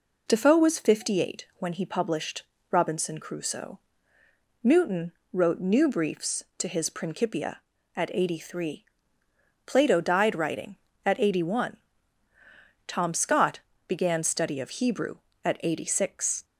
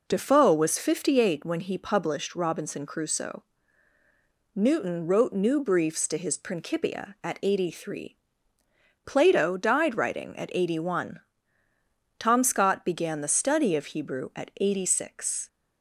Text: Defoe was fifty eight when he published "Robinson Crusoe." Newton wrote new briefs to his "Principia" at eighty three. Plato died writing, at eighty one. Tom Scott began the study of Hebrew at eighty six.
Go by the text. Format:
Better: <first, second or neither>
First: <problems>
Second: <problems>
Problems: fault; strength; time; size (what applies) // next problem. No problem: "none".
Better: second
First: pauses between "published" and "Robinson"; slight; at 2.4 s; 0.30 s long // pauses between "Newton" and "wrote"; slight; at 5.1 s; 0.20 s long // pauses between "Scott" and "began"; slight; at 13.6 s; 0.26 s long // skips "the"; at 14.2 s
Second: none